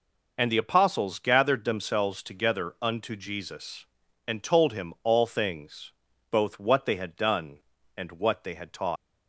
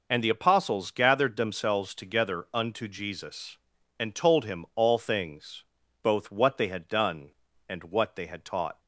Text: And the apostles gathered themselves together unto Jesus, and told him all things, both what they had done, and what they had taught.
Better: second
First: leaves "taught" unfinished; at 8.9 s; 115 ms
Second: none

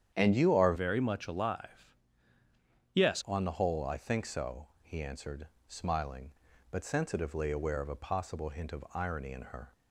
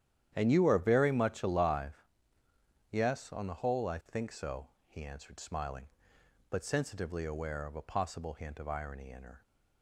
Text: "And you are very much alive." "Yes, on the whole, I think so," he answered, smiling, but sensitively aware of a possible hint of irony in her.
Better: second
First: starts louder than the rest; strong; until 1.1 s; 9 dB // changes voice from "very" to "Yes"; from 0.7 to 3.2 s; 2.5 s long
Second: starts louder than the rest; strong; until 1.3 s; 10.5 dB

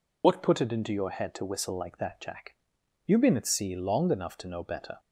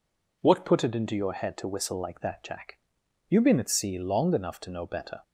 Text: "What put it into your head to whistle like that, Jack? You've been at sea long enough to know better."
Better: second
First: loses the start of "What"; at 0.2 s; 70 ms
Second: none

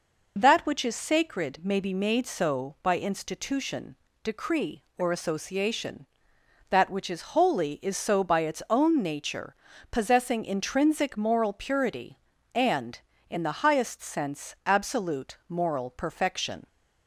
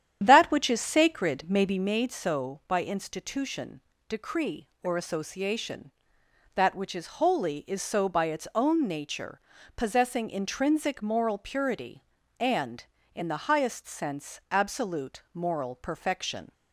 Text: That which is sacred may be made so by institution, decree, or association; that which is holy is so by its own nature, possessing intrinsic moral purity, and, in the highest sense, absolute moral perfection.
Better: first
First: none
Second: starts louder than the rest; strong; until 2.0 s; 10 dB

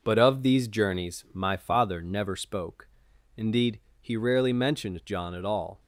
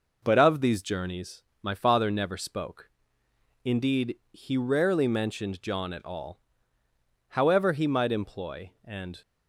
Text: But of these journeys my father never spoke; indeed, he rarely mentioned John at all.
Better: first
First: none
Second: pauses between "journeys" and "my"; slight; at 1.4 s; 0.20 s long // goes on to say "However he might employ and"; strong; from 7.2 s on; 1.9 s long

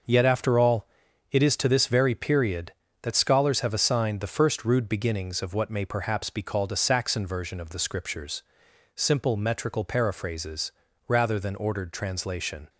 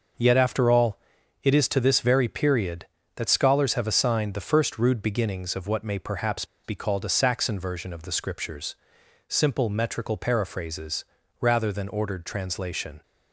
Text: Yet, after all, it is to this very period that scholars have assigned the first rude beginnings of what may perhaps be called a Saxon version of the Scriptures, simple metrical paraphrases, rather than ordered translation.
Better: first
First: none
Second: pauses between "perhaps" and "be"; slight; at 6.4 s; 0.19 s long

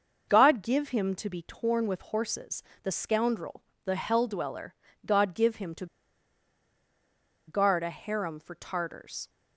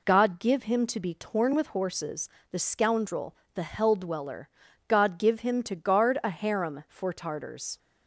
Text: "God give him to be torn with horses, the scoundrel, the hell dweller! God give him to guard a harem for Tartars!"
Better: second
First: pauses between "to" and "guard"; strong; at 5.8 s; 1.6 s long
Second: none

